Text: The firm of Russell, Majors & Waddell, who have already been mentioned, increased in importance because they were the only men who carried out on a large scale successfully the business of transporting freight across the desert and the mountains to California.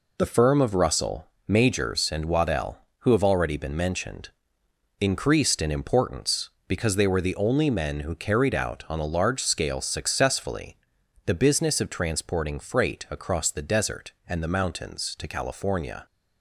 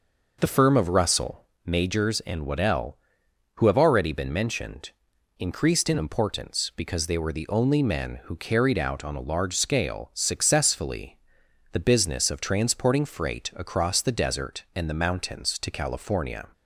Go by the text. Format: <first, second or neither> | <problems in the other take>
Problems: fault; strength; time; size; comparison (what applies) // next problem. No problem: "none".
neither | pauses between "successfully" and "the"; noticeable; the same in both